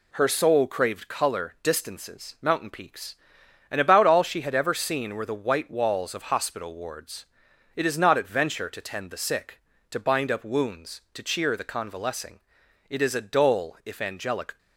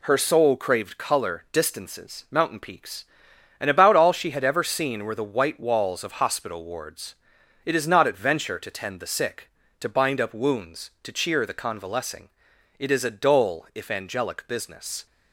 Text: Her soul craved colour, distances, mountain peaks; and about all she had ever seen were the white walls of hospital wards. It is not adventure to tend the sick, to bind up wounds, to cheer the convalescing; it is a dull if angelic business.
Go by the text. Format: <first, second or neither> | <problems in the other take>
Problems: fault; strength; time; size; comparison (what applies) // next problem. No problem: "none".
second | stops before "business"; at 14.5 s